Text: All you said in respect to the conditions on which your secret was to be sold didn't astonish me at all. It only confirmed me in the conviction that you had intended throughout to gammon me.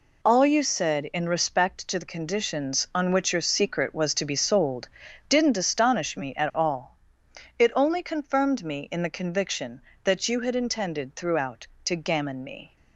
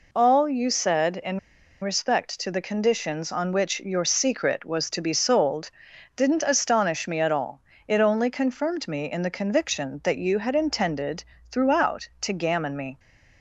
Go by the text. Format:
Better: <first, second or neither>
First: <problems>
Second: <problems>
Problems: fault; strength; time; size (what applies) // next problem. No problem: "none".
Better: first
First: pauses between "sold" and "didn't"; at 4.8 s; 0.42 s long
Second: pauses between "in" and "respect"; at 1.3 s; 0.42 s long // pauses between "sold" and "didn't"; at 5.7 s; 0.44 s long // pauses between "intended" and "throughout"; slight; at 11.2 s; 0.28 s long